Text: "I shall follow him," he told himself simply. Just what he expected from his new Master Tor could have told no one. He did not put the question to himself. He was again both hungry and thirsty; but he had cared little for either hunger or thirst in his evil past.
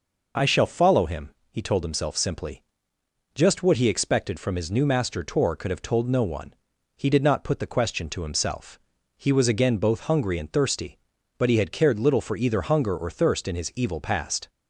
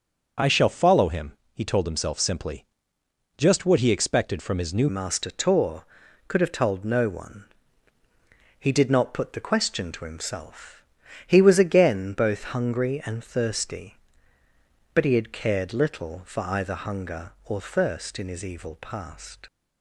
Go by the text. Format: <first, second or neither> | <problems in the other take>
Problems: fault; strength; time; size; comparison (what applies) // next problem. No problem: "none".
first | starts louder than the rest; until 1.6 s; 6 dB // changes voice at "Master"; from 4.8 s on; 14.6 s long